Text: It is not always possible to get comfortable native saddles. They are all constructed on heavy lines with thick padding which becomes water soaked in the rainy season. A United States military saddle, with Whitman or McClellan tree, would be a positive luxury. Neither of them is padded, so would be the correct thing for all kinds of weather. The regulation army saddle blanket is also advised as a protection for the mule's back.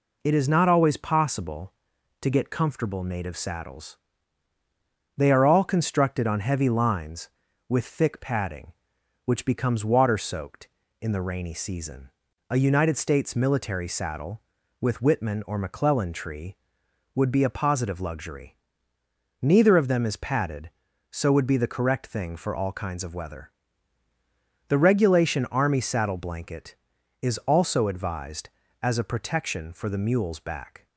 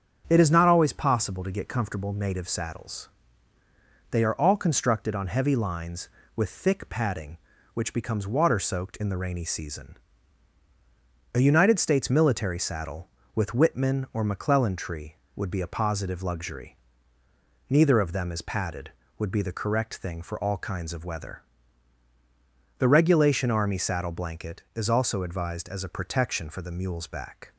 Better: first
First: none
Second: starts louder than the rest; strong; until 1.2 s; 8 dB // skips "so"; at 19.0 s

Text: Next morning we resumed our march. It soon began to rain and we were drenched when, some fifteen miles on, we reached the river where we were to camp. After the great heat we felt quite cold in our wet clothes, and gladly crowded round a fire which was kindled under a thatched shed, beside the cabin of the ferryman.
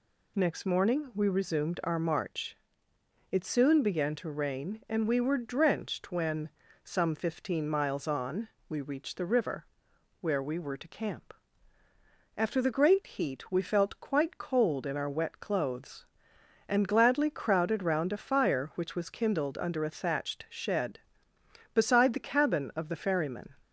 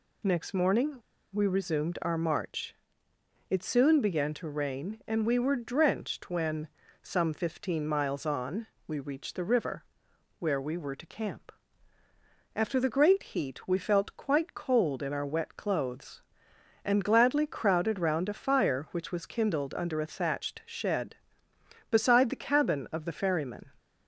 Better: first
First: pauses between "river" and "where"; noticeable; at 9.6 s; 0.54 s long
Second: pauses between "morning" and "we"; slight; at 0.9 s; 0.34 s long // pauses between "river" and "where"; noticeable; at 9.8 s; 0.54 s long

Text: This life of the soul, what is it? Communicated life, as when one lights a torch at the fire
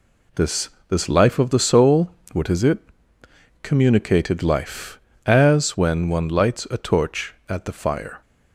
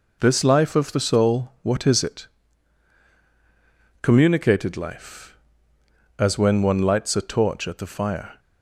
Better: second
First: says "This" twice; at 0.8 s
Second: none

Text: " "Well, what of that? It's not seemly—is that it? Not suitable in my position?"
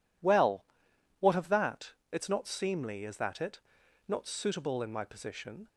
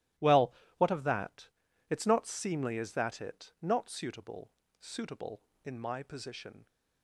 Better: first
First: none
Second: starts louder than the rest; strong; until 1.4 s; 14.5 dB // says "suitable" twice; at 4.7 s

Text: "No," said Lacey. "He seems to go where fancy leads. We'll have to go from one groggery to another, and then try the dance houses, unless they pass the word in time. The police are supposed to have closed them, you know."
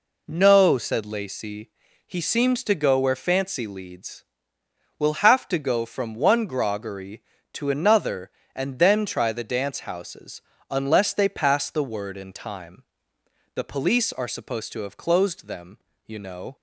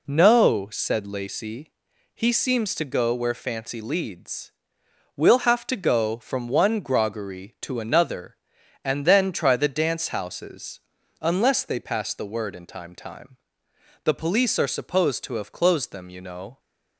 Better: first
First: none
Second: says "time" twice; at 12.9 s

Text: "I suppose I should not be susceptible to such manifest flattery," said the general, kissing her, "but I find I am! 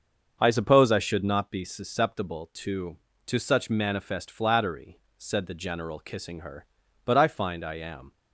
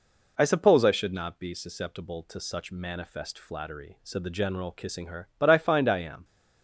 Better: second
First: starts louder than the rest; until 1.4 s; 6.5 dB // says "to" twice; at 3.2 s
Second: none

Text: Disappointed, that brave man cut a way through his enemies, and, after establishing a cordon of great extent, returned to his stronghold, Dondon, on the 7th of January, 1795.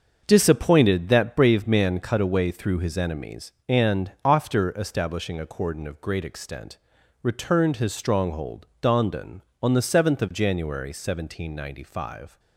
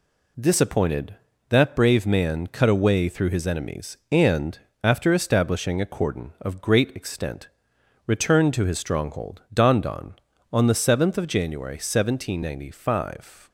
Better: second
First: starts louder than the rest; until 1.2 s; 6.5 dB // skips "to"; at 7.7 s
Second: none

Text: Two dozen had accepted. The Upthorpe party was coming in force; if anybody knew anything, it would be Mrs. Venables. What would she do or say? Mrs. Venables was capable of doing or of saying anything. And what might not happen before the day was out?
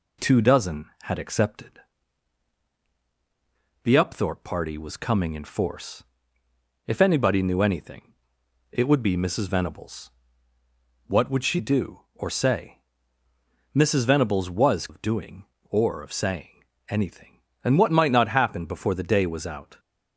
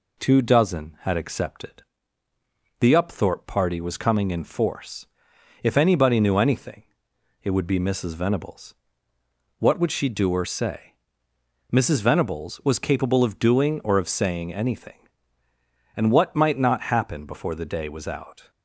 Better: second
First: skips "capable"; at 14.8 s // pauses between "saying" and "anything"; slight; at 16.6 s; 0.24 s long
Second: none

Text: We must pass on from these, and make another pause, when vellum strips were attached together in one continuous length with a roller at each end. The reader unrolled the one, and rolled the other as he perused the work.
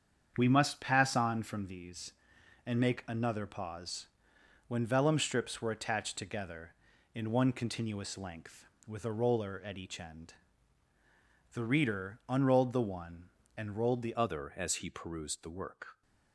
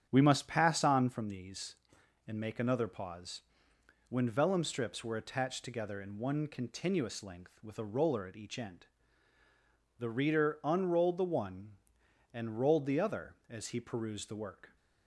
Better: second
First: starts louder than the rest; strong; until 1.3 s; 7.5 dB // changes voice at "other"; from 14.1 s on; 1.9 s long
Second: starts louder than the rest; strong; until 1.1 s; 8.5 dB

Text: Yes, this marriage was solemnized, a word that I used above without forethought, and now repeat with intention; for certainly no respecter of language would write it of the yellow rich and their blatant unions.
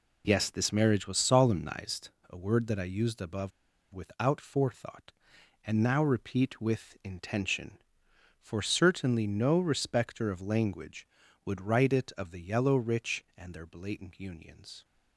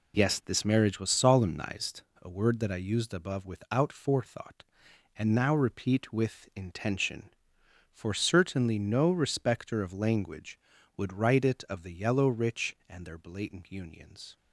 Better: second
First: pauses between "above" and "without"; at 3.5 s; 0.43 s long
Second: none

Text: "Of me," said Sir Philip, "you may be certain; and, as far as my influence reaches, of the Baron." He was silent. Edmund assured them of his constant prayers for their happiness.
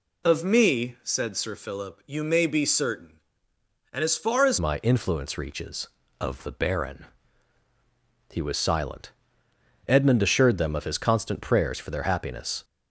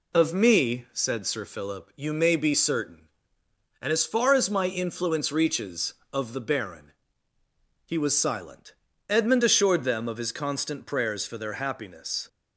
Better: second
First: changes voice at "my"; from 4.5 s on; 8.1 s long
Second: none

